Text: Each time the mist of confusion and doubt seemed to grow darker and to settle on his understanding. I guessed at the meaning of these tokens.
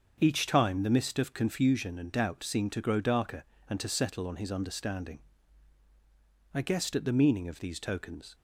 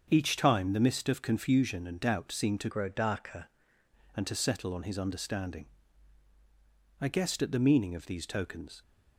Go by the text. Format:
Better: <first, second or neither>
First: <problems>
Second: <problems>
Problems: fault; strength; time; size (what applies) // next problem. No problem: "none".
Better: first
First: starts louder than the rest; until 1.2 s; 7 dB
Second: starts louder than the rest; until 1.1 s; 7 dB // changes voice from "grow" to "darker"; from 2.6 to 3.4 s; 0.8 s long